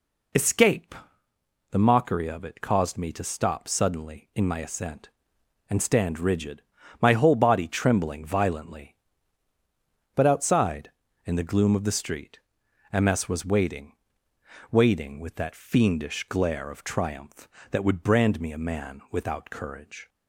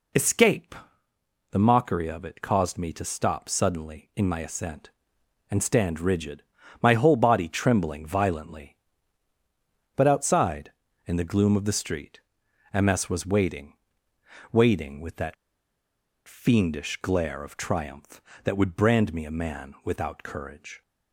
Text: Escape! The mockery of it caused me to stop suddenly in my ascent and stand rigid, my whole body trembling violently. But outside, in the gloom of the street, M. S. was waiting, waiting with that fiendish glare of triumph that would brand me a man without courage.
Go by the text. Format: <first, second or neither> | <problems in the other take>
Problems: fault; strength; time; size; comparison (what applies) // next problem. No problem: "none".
first | pauses between "that" and "fiendish"; noticeable; at 15.3 s; 0.92 s long